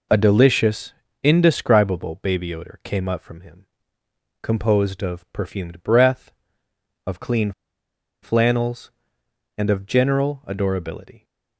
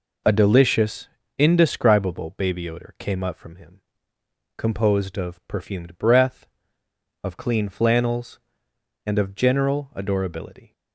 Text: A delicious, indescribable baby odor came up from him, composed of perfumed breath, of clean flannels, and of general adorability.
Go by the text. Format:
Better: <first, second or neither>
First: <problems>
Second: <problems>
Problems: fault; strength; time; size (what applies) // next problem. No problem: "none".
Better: second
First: pauses between "clean" and "flannels"; noticeable; at 7.5 s; 0.71 s long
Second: none